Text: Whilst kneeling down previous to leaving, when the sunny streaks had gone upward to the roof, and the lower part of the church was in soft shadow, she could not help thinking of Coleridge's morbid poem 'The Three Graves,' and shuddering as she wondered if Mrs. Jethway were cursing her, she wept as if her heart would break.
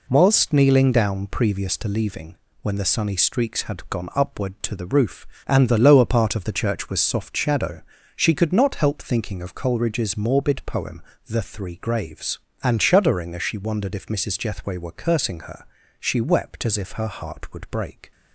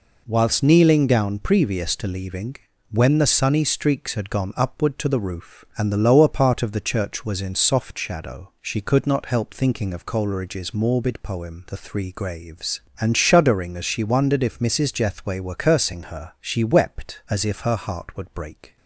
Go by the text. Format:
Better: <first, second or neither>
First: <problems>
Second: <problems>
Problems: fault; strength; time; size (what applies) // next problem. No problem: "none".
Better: second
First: skips "in"; at 6.9 s // pauses between "poem" and "The"; slight; at 11.0 s; 0.26 s long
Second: none